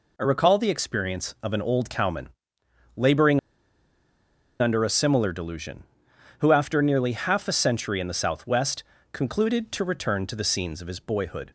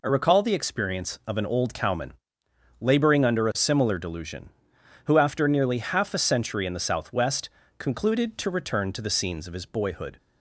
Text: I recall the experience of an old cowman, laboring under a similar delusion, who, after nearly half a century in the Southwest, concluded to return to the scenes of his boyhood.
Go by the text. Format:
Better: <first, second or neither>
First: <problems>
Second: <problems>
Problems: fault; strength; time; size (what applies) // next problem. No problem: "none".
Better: second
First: pauses between "laboring" and "under"; at 3.3 s; 1.2 s long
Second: none